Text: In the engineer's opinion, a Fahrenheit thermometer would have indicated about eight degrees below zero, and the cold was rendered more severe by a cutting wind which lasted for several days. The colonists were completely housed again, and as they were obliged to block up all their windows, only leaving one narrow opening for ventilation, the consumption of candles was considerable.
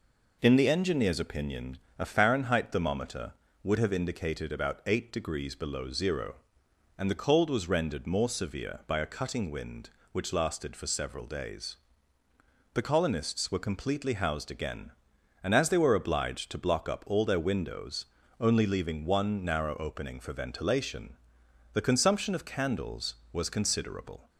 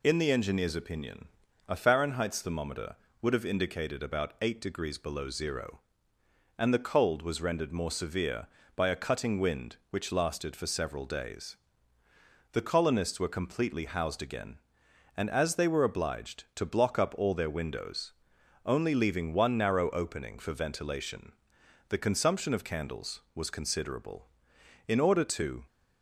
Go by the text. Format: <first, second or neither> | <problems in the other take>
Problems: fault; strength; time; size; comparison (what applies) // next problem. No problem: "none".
first | goes on to say "In order to"; noticeable; from 24.8 s on; 0.78 s long